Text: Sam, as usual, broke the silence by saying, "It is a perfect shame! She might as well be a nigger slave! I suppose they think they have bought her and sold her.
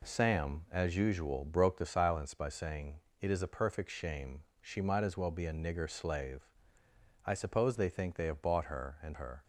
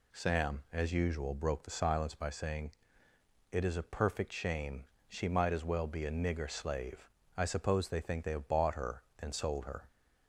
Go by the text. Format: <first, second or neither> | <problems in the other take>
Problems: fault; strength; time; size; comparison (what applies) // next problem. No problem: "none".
second | skips "sold"; at 9.1 s